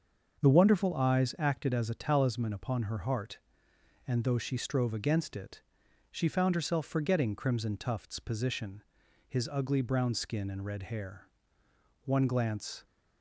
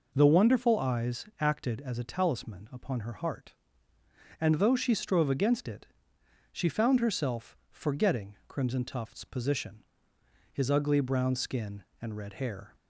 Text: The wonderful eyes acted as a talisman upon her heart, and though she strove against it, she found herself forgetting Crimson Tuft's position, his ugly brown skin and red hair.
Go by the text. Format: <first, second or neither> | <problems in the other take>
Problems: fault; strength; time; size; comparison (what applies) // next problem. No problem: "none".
second | starts louder than the rest; until 1.4 s; 6.5 dB // goes on to say "One glance"; noticeable; from 12.0 s on; 0.80 s long